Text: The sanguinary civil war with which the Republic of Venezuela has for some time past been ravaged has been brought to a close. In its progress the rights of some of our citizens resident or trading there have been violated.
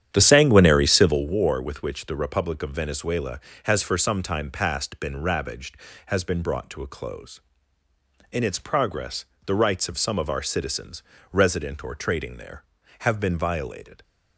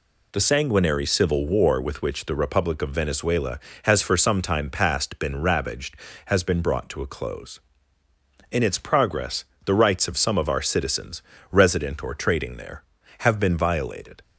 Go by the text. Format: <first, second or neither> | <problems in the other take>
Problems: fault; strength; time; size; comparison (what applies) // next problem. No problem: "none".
second | starts louder than the rest; strong; until 1.3 s; 9.5 dB // pauses between "progress" and "the"; slight; at 9.2 s; 0.20 s long; slight in the second // pauses between "citizens" and "resident"; slight; at 11.0 s; 0.28 s long; slight in the second